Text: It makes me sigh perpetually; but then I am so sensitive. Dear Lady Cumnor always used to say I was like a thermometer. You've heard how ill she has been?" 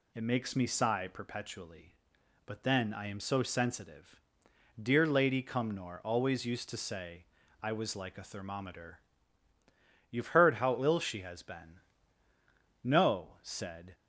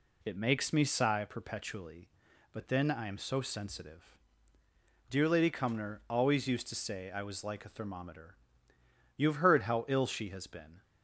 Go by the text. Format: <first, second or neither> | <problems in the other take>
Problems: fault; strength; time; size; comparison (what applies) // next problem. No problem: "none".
second | pauses between "say" and "I"; at 7.2 s; 0.38 s long // goes on to say "No said"; noticeable; from 12.8 s on; 1.1 s long